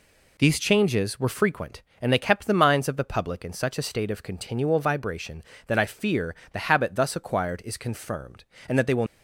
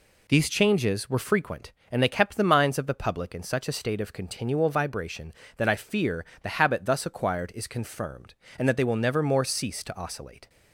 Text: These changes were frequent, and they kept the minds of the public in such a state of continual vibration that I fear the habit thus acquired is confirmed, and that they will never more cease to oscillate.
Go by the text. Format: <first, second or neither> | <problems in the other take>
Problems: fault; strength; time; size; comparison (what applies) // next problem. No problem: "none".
second | pauses between "fear" and "the"; slight; at 6.3 s; 0.16 s long; slight in the second // stops before "never more cease to oscillate"; at 9.0 s